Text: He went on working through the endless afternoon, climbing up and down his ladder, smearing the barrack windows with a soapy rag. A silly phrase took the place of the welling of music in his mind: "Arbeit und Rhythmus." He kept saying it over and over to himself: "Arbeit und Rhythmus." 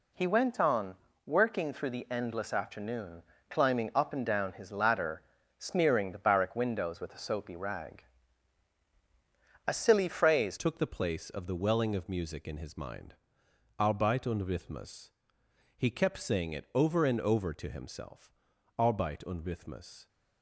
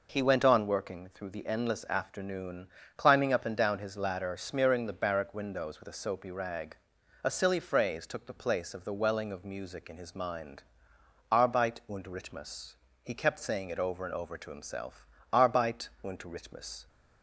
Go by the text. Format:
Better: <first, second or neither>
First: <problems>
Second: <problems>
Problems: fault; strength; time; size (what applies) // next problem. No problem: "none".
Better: second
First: pauses between "on" and "working"; slight; at 0.9 s; 0.32 s long // changes voice at "took"; from 10.5 s on; 9.5 s long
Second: none